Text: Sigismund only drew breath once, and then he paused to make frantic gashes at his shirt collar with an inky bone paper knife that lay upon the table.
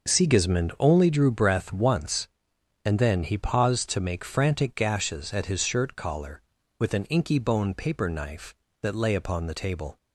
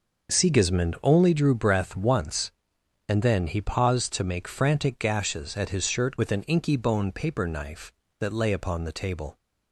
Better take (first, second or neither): first